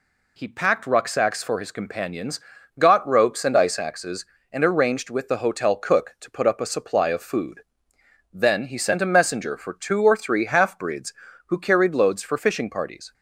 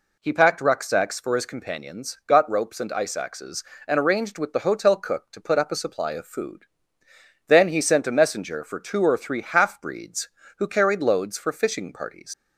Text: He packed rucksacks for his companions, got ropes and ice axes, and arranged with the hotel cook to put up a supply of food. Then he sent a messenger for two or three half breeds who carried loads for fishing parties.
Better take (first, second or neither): first